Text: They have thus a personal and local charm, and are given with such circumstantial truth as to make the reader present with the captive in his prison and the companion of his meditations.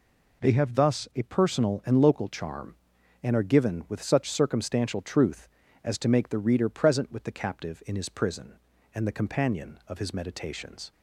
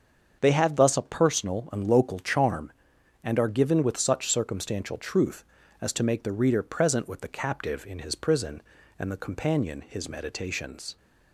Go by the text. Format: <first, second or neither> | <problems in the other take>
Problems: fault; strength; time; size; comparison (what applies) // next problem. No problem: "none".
first | starts louder than the rest; until 1.4 s; 7 dB // skips "of"; at 9.8 s